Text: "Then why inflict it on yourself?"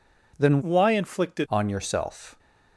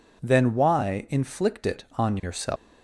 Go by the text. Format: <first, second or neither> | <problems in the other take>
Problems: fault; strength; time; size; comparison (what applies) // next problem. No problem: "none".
second | changes voice from "why" to "it"; from 0.6 to 1.4 s; 0.8 s long